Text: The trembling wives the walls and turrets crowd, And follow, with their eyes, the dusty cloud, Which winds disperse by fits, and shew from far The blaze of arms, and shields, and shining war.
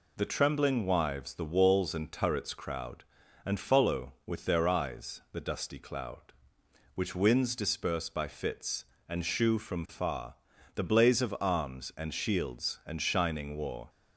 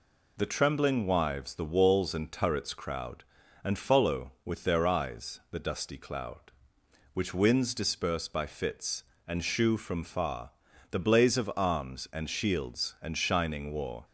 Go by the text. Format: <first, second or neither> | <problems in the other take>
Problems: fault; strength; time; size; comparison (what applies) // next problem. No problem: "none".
neither | pauses between "far" and "The"; the same in both